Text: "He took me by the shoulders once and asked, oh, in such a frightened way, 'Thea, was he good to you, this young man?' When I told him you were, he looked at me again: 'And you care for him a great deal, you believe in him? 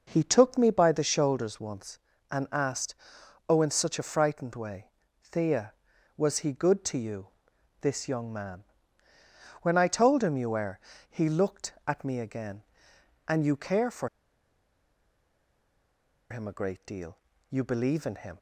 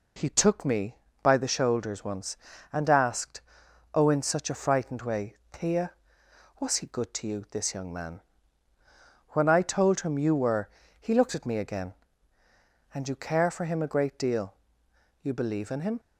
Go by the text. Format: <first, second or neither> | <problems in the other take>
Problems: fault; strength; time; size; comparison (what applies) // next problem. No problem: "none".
second | pauses between "for" and "him"; strong; at 14.0 s; 2.2 s long